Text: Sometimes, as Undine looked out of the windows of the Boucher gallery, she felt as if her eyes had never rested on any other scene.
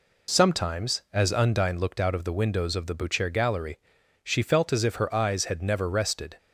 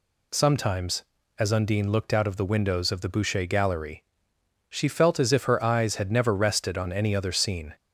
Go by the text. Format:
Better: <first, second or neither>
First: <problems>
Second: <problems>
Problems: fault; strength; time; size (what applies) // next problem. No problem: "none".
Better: second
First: stops before "on any other scene"; at 6.3 s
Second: none